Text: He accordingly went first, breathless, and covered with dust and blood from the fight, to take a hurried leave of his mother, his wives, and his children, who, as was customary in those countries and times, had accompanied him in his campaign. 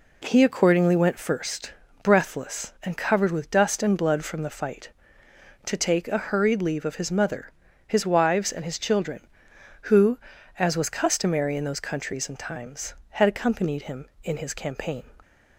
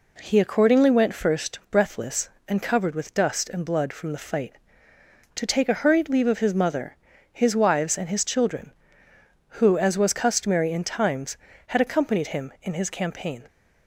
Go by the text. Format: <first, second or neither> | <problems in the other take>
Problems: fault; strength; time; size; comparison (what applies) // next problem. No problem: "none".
first | skips "those countries and"; at 10.8 s